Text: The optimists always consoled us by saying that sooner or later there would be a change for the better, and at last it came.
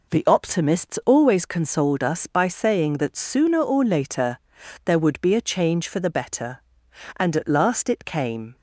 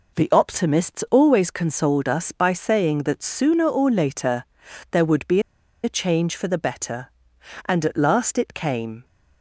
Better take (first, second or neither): first